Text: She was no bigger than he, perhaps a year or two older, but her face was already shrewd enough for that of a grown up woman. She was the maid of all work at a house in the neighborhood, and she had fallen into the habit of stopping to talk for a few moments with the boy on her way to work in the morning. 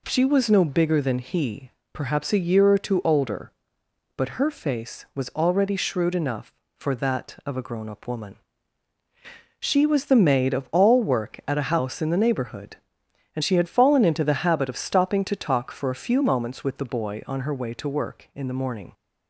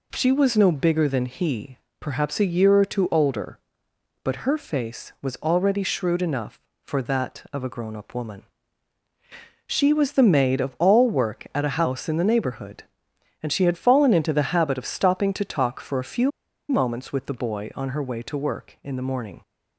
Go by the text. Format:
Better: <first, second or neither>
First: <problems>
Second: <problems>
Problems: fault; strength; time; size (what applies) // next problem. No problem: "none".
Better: first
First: none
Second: pauses between "few" and "moments"; at 16.2 s; 0.39 s long